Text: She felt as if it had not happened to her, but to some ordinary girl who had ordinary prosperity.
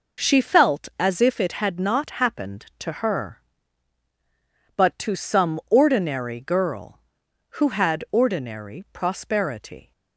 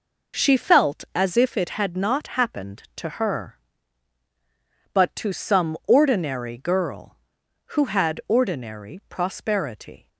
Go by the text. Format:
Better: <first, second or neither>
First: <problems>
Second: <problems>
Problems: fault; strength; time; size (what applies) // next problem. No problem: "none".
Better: neither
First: none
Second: none